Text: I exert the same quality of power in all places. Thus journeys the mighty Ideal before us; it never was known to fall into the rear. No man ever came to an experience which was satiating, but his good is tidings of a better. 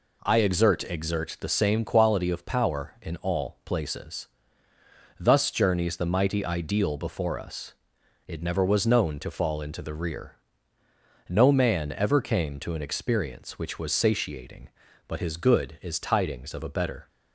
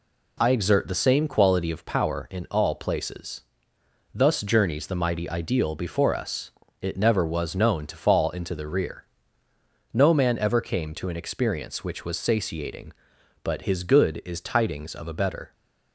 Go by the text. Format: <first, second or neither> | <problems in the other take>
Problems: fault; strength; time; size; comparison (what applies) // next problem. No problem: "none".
second | says "exert" twice; at 0.8 s